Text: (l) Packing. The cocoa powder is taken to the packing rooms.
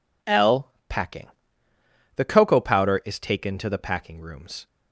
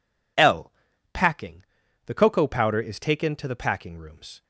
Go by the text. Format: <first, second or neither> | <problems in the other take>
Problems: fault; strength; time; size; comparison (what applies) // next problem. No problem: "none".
neither | none